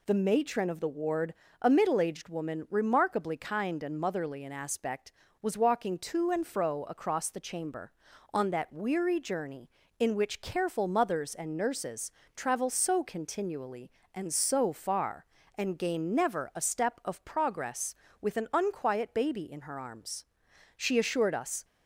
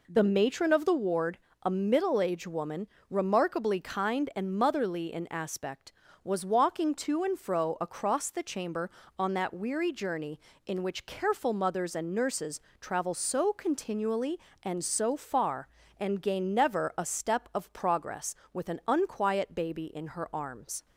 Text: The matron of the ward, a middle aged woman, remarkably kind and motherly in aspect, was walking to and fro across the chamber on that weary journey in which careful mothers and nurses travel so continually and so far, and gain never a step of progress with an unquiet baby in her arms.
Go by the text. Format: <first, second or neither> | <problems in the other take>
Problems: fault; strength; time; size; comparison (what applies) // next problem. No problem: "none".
second | pauses between "nurses" and "travel"; slight; at 12.1 s; 0.24 s long; slight in the second // goes on to say "She assured us"; noticeable; from 20.7 s on; 0.88 s long